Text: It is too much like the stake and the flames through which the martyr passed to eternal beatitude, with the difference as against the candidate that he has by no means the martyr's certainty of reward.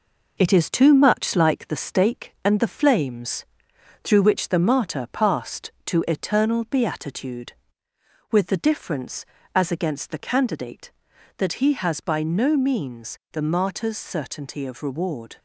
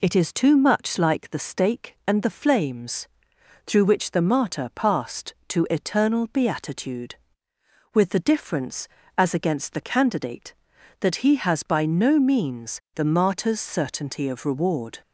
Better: second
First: gets quieter; noticeable; throughout; 4.5 dB // pauses between "flames" and "through"; noticeable; at 3.4 s; 0.60 s long // pauses between "means" and "the"; slight; at 13.1 s; 0.16 s long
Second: pauses between "flames" and "through"; noticeable; at 3.0 s; 0.60 s long // pauses between "means" and "the"; slight; at 12.7 s; 0.16 s long

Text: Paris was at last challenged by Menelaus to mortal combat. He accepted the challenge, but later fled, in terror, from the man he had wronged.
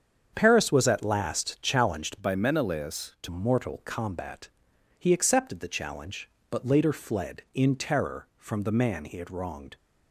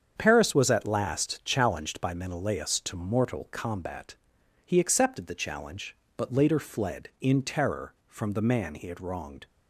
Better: second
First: starts louder than the rest; strong; until 1.3 s; 7.5 dB // changes voice from "by" to "to"; from 2.1 to 3.2 s; 1.1 s long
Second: starts louder than the rest; strong; until 1.1 s; 7.5 dB

